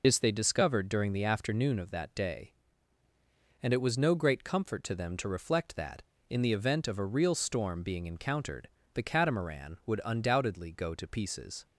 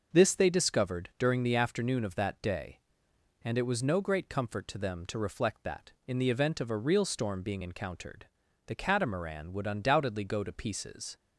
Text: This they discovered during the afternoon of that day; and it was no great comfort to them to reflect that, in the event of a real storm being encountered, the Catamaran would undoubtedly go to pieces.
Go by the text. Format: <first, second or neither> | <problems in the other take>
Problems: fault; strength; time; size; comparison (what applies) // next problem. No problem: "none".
second | loses the start of "This"; at 0.0 s; 55 ms